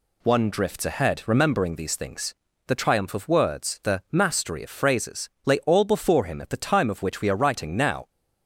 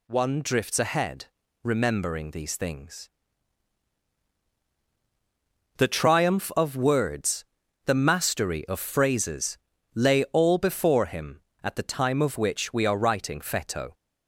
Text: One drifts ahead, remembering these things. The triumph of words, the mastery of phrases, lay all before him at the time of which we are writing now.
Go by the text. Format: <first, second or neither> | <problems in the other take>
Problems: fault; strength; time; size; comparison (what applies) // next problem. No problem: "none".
first | says "feto" for "now"; at 13.3 s